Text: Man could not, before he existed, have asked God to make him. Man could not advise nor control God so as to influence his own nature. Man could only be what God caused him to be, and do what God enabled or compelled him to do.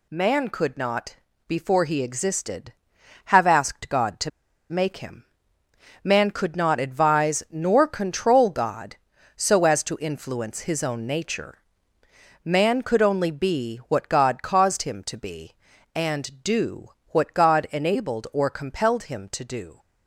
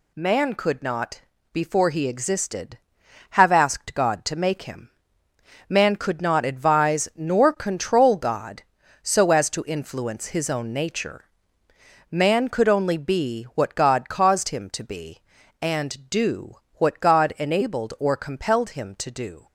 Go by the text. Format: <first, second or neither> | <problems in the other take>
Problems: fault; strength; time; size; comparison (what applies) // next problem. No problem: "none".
second | pauses between "to" and "make"; at 4.2 s; 0.40 s long // pauses between "do" and "what"; slight; at 16.8 s; 0.18 s long; slight in the second